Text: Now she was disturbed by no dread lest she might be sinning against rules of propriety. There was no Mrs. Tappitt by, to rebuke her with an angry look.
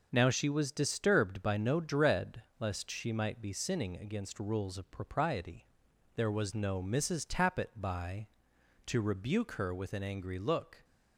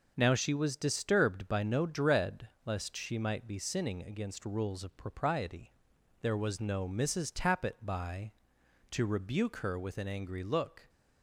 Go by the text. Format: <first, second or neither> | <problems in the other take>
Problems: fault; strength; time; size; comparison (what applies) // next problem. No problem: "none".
neither | pauses between "dread" and "lest"; slight; the same in both